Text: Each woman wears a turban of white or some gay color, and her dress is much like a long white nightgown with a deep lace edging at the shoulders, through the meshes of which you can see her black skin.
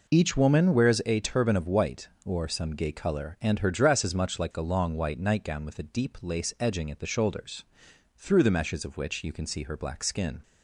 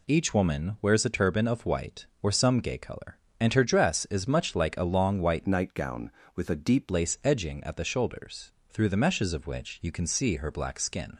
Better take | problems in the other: first | changes voice from "nightgown" to "deep"; from 5.4 to 6.9 s; 1.5 s long

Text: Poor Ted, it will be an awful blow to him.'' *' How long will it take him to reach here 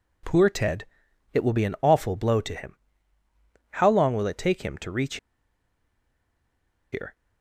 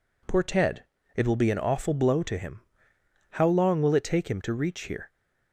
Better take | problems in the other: second | pauses between "reach" and "here"; strong; at 5.1 s; 1.7 s long

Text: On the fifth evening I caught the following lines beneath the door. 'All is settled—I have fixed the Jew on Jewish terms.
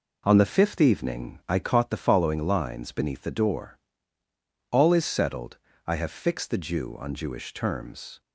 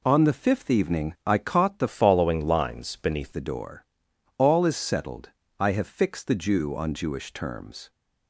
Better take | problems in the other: first | changes voice from "following" to "beneath"; from 1.8 to 3.3 s; 1.5 s long

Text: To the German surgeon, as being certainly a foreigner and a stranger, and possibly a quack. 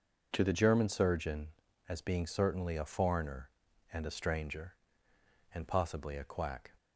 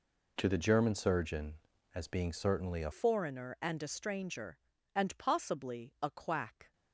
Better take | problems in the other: first | changes voice at "foreigner"; from 2.9 s on; 3.8 s long

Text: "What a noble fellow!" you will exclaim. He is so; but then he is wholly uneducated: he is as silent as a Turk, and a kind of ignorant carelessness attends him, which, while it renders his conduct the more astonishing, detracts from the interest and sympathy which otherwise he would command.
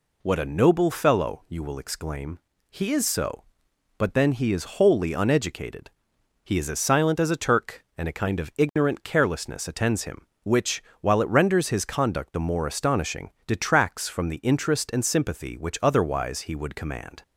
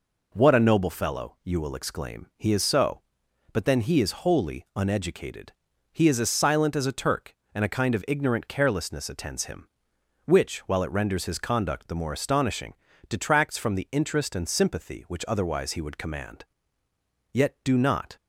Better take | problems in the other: first | goes on to say "Yet do not"; noticeable; from 17.3 s on; 0.82 s long

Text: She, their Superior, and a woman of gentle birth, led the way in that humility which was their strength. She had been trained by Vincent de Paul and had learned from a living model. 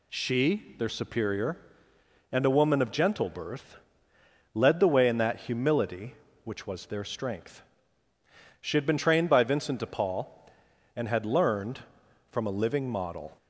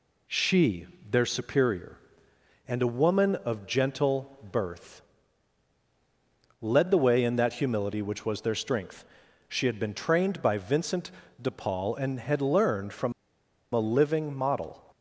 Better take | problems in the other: first | pauses between "gentle" and "birth"; slight; at 4.3 s; 0.16 s long // pauses between "Vincent" and "de"; slight; at 11.1 s; 0.30 s long // pauses between "from" and "a"; noticeable; at 13.1 s; 0.62 s long

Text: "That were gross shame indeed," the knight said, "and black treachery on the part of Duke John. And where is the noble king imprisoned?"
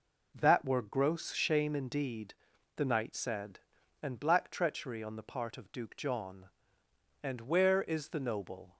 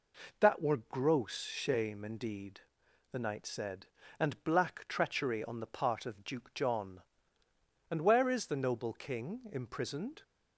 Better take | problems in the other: second | stops before "king imprisoned"; at 8.7 s

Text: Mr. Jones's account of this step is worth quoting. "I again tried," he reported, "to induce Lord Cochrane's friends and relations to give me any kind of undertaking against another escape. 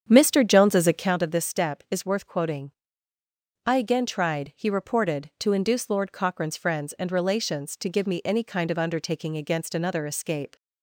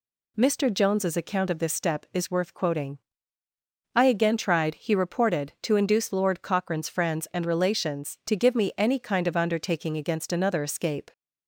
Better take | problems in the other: second | starts louder than the rest; strong; until 1.2 s; 8 dB

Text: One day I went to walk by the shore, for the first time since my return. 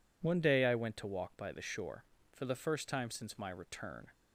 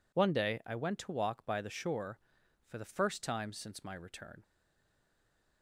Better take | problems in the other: first | stays silent after the last word; noticeable; from 4.4 s on; 1.2 s long

